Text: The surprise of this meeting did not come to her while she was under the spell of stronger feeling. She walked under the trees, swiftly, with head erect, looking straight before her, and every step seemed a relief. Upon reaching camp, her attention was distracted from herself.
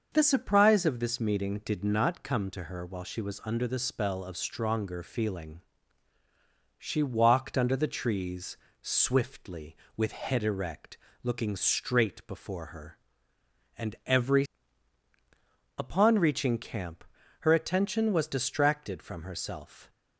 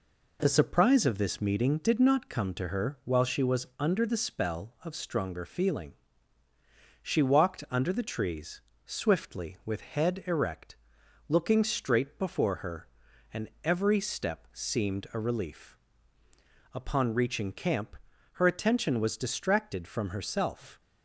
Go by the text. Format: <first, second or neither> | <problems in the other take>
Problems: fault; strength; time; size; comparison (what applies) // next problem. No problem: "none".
second | starts louder than the rest; until 1.1 s; 6 dB // skips "step seemed a relief"; at 15.1 s